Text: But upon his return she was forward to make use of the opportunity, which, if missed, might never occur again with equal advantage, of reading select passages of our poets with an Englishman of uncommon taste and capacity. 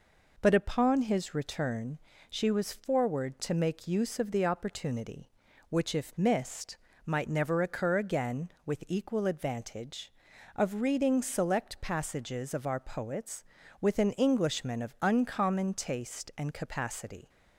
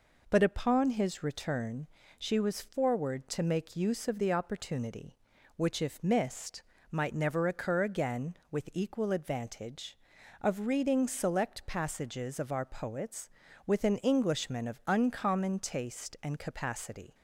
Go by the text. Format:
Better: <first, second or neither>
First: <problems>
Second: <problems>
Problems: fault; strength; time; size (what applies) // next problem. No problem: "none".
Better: neither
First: pauses between "return" and "she"; slight; at 1.9 s; 0.32 s long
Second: pauses between "return" and "she"; slight; at 1.8 s; 0.32 s long